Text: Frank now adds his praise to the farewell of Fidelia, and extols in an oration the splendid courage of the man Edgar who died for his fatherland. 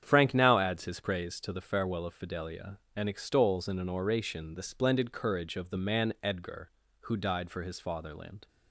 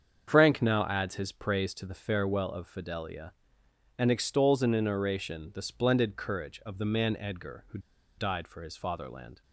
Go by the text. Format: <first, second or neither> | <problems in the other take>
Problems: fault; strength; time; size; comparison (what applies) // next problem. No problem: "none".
first | starts louder than the rest; strong; until 1.2 s; 7.5 dB; strong in the first // pauses between "who" and "died"; at 7.7 s; 0.38 s long